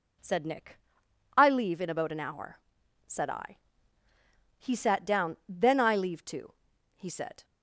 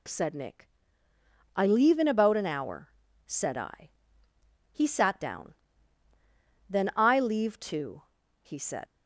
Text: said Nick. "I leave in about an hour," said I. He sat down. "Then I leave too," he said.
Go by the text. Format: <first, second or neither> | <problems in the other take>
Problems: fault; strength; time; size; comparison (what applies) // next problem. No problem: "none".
first | leaves "said" unfinished; at 8.8 s; 125 ms